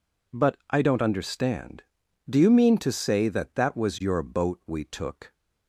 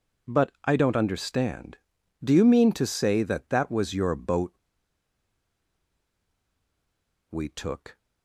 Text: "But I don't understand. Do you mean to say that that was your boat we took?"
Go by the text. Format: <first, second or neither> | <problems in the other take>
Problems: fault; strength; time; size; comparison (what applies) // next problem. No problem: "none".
first | pauses between "boat" and "we"; strong; at 4.5 s; 2.7 s long